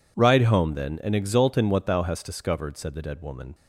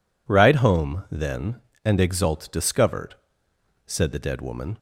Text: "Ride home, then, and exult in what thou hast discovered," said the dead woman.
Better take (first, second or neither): first